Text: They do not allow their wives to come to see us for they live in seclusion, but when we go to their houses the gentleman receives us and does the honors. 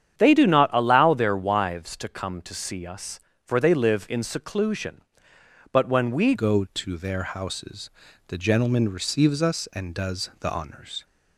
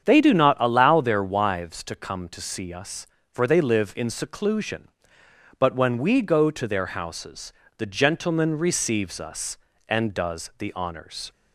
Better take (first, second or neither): second